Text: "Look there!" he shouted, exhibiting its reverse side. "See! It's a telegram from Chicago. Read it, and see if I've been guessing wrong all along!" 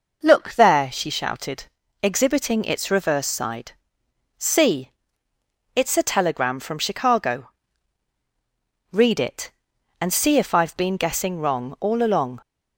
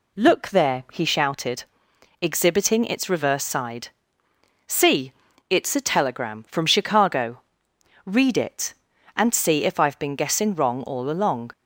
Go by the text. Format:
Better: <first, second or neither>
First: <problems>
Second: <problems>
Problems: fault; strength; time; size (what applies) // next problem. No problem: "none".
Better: second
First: says "she" for "he"; at 0.9 s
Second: none